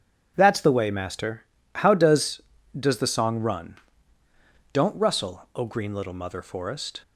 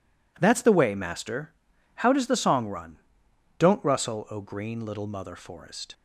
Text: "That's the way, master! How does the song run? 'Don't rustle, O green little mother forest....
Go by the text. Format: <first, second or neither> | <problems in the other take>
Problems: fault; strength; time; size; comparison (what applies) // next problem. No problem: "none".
second | says "does" twice; at 2.7 s